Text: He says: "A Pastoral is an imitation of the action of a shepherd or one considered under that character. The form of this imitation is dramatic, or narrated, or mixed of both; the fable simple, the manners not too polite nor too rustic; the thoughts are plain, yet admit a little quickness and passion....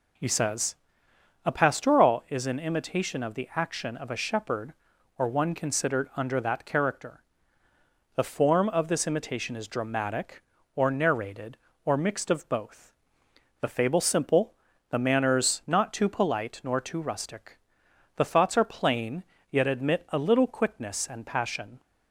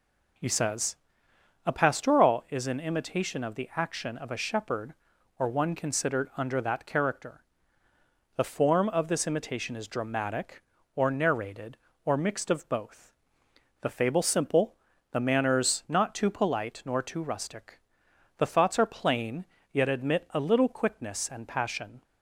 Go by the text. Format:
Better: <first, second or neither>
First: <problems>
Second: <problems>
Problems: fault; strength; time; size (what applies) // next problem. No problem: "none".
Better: neither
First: none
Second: none